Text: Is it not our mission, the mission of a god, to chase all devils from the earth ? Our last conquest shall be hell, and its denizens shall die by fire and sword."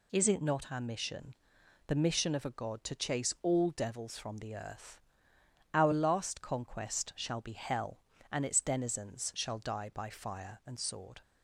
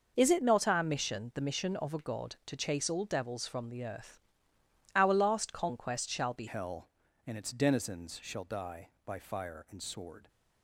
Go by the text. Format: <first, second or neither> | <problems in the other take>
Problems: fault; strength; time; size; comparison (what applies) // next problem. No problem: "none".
first | changes voice at "hell"; from 6.4 s on; 3.8 s long